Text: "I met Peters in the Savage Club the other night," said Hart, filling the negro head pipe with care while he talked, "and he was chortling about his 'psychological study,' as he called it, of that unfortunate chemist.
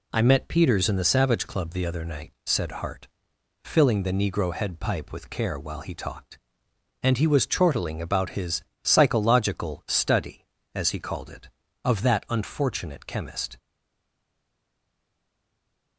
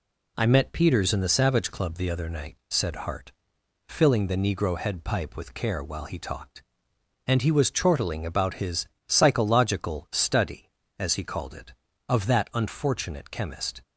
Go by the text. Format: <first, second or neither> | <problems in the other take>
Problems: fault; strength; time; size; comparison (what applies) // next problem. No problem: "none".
second | pauses between "his" and "psychological"; slight; at 8.6 s; 0.18 s long; slight in the second // stays silent after the last word; from 13.5 s on; 2.4 s long